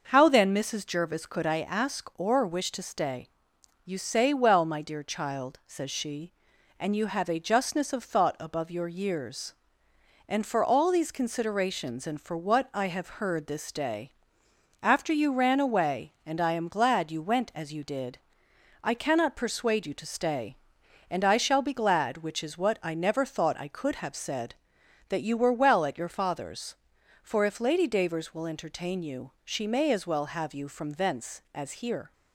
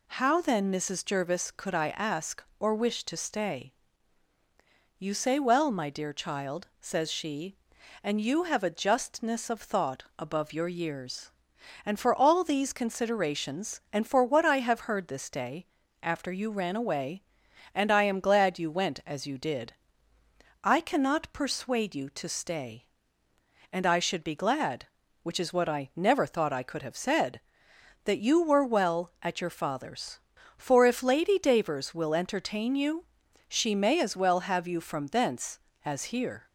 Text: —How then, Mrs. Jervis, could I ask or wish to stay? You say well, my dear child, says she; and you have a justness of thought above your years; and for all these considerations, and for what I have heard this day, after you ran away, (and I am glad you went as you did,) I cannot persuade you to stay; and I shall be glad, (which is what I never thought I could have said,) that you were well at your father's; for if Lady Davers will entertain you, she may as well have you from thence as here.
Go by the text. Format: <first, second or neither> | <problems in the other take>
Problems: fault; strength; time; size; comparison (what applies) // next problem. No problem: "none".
first | says "should" for "shall"; at 23.9 s